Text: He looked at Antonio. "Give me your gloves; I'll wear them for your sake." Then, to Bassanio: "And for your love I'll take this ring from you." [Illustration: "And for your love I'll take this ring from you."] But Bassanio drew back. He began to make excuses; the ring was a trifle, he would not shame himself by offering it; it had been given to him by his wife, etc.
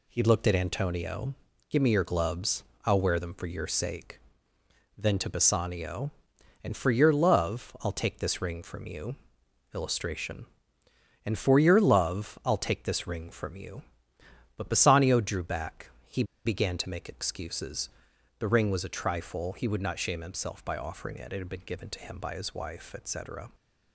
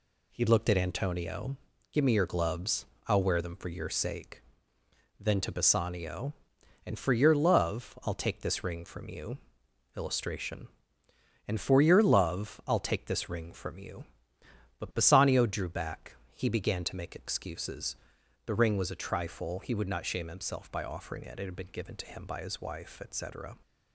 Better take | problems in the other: second | pauses between "He" and "began"; slight; at 16.2 s; 0.21 s long

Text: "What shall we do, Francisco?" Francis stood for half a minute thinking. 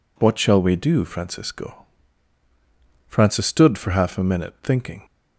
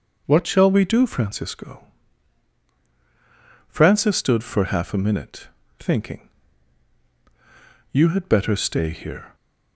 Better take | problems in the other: first | starts louder than the rest; noticeable; until 1.2 s; 6 dB // pauses between "minute" and "thinking"; slight; at 5.4 s; 0.30 s long // goes on to say "You had better stay here"; from 7.9 s on; 1.4 s long

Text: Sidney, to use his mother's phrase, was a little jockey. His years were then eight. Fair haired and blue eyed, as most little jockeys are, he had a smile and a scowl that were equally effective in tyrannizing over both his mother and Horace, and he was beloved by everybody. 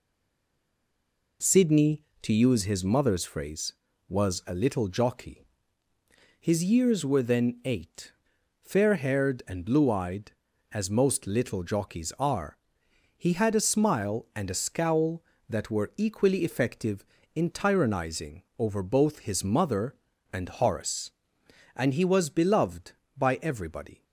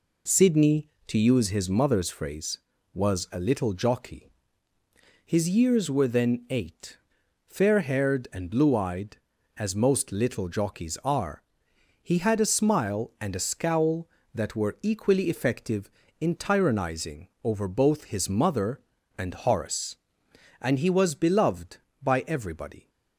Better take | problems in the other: second | stays silent before the first word; noticeable; until 1.4 s; 1.4 s long // pauses between "tyrannizing" and "over"; slight; at 18.4 s; 0.16 s long; slight in the second

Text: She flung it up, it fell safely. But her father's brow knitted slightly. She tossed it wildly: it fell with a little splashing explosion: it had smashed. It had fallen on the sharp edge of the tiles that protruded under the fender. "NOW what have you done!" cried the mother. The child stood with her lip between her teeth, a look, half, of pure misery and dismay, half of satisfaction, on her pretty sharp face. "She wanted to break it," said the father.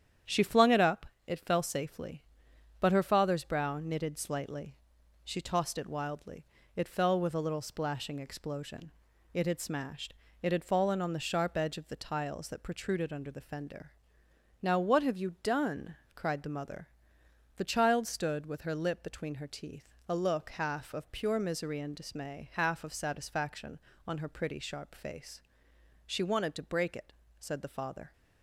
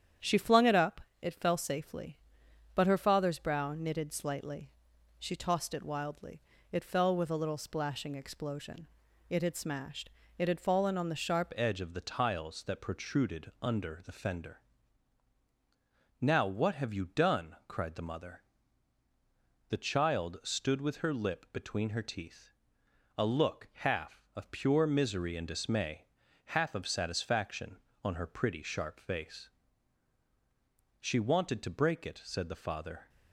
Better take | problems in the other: first | starts louder than the rest; strong; until 1.4 s; 9 dB; strong in the first // changes voice at "edge"; from 11.5 s on; 21.5 s long

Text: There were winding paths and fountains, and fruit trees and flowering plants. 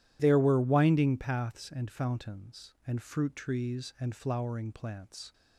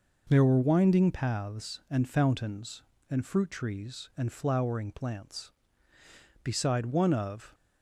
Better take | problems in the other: first | goes on to say "Beside one of"; noticeable; from 6.4 s on; 1.1 s long

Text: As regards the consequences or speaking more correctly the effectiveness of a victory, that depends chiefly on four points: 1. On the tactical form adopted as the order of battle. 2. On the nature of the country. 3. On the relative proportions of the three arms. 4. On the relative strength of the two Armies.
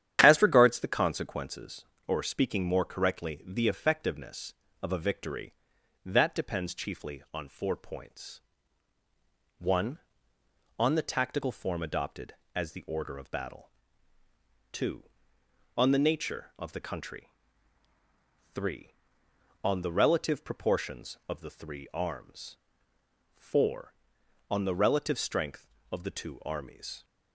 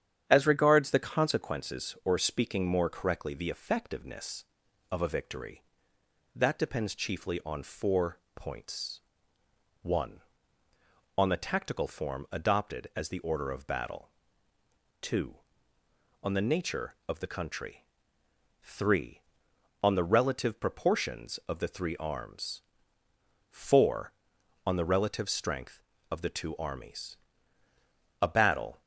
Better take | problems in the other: first | starts louder than the rest; strong; until 1.3 s; 9 dB; strong in the first // pauses between "four" and "points"; slight; at 8.1 s; 0.16 s long // goes on to say "A battle"; from 28.2 s on; 0.60 s long

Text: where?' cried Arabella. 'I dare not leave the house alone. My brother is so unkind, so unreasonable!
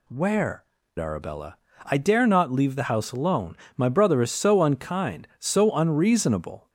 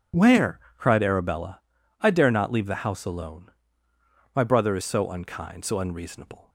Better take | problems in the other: second | skips "cried"; at 0.8 s

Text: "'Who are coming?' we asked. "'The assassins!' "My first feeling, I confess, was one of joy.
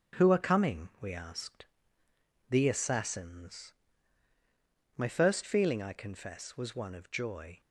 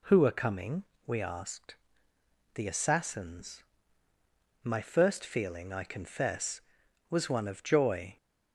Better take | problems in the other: second | gets quieter; noticeable; throughout; 5.5 dB

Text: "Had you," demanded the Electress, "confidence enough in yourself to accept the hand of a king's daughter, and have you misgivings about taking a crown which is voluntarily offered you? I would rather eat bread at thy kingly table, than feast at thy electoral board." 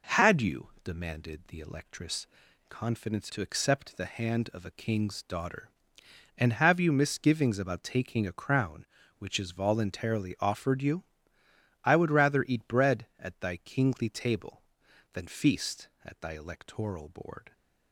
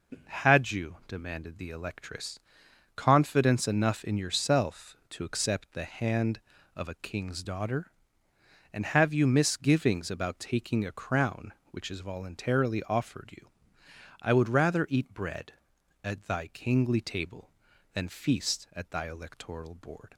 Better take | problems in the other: second | skips "enough in yourself"; at 3.3 s

